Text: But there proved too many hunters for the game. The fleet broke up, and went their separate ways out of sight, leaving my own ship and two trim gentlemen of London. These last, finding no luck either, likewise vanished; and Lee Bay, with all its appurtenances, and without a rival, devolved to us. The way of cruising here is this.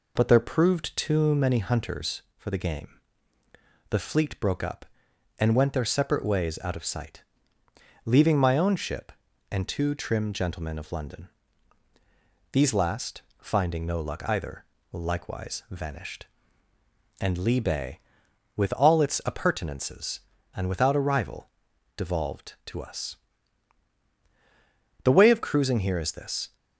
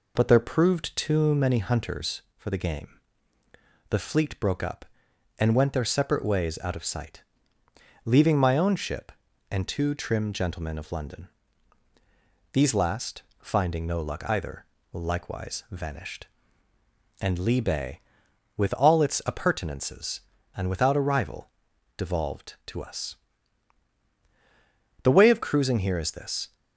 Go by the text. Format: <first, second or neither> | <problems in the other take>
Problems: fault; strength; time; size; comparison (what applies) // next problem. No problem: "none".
neither | none